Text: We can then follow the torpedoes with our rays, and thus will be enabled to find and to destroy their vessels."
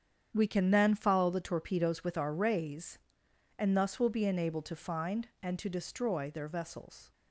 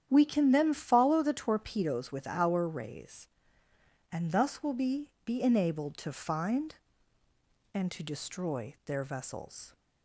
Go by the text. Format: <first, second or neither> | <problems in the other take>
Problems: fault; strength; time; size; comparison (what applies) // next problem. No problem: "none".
first | starts louder than the rest; strong; until 1.1 s; 9.5 dB; strong in the first // says "be" twice; at 5.2 s